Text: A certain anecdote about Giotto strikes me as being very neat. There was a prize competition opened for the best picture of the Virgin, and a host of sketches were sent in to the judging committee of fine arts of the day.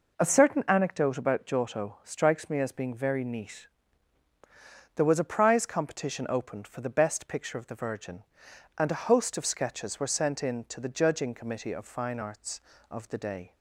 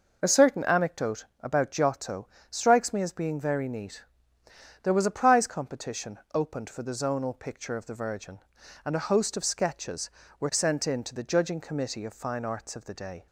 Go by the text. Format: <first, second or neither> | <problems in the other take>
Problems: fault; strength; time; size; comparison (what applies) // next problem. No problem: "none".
first | pauses between "Giotto" and "strikes"; slight; at 2.2 s; 0.22 s long // pauses between "competition" and "opened"; slight; at 6.1 s; 0.16 s long // says "zonal" for "best"; at 6.9 s